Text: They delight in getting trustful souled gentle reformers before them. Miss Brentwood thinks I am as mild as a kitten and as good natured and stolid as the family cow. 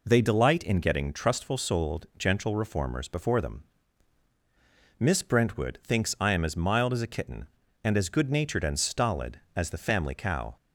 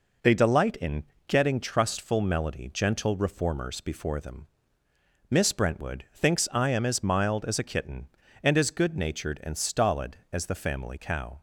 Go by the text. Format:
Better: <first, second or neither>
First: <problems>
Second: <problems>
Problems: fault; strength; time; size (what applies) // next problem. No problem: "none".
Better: first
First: none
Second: pauses between "in" and "getting"; slight; at 1.0 s; 0.24 s long // says "melody" for "souled"; at 2.2 s